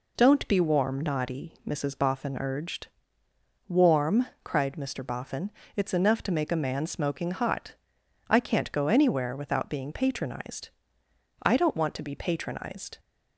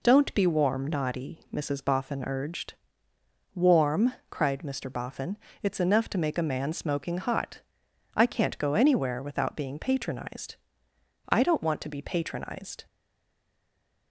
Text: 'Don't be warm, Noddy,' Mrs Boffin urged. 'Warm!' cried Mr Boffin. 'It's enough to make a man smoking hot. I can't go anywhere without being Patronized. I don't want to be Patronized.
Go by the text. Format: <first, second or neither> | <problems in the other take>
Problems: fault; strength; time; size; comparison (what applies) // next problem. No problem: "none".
first | stays silent after the last word; noticeable; from 12.8 s on; 1.3 s long